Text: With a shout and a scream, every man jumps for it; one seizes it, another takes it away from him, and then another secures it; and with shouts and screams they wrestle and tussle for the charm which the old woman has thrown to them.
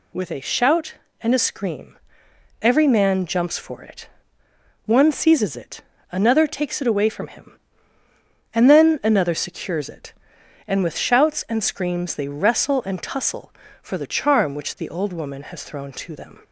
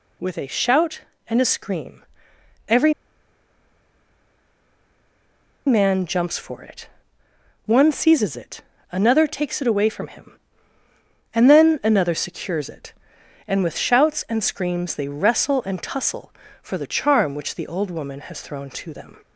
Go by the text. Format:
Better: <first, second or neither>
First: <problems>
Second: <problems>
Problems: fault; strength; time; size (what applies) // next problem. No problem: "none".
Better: first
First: none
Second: pauses between "every" and "man"; strong; at 2.9 s; 2.7 s long